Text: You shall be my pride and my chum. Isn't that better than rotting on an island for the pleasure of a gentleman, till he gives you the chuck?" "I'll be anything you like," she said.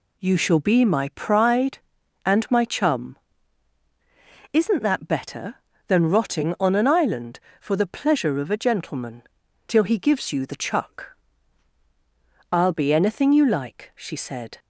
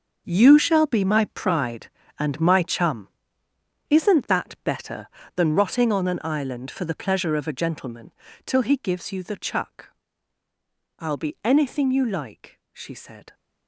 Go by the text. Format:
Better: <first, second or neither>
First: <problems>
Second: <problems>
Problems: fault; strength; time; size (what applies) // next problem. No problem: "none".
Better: first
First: none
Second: gets quieter; strong; throughout; 16 dB